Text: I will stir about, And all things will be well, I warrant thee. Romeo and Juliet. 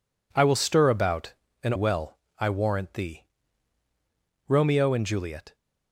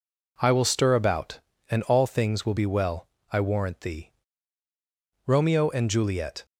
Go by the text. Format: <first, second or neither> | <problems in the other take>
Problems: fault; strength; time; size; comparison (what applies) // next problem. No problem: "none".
second | skips "all things will be"; at 1.7 s